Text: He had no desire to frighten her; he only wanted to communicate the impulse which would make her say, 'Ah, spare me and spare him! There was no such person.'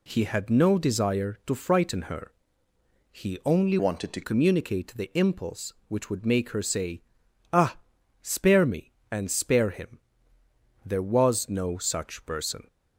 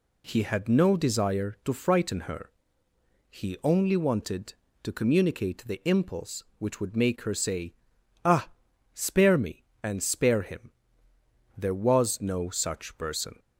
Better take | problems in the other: second | changes voice from "wanted" to "to"; from 3.7 to 4.2 s; 0.5 s long

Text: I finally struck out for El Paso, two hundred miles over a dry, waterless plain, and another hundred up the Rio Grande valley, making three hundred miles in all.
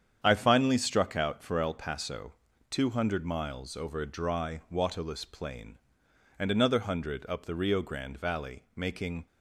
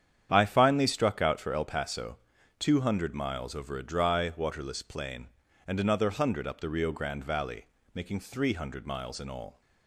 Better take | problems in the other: second | starts louder than the rest; strong; until 1.2 s; 8.5 dB; strong in the second // stops before "three hundred miles in all"; at 9.2 s

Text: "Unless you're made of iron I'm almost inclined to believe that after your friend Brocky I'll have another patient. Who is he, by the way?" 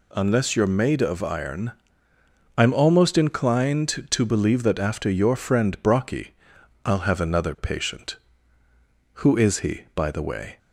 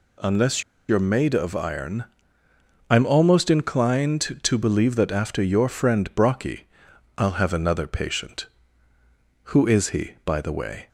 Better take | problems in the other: first | pauses between "Unless" and "you're"; slight; at 0.6 s; 0.27 s long // pauses between "iron" and "I'm"; noticeable; at 2.0 s; 0.86 s long; noticeable in the first // pauses between "Brocky" and "I'll"; noticeable; at 6.6 s; 0.50 s long; noticeable in the first

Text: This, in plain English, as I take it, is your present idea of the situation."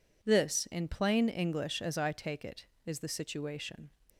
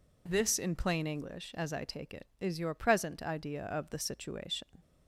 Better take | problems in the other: second | skips "your present idea of"; at 2.9 s

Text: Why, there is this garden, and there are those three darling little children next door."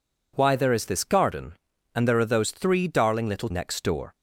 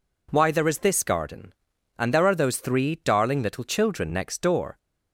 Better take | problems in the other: second | skips "children"; at 3.5 s

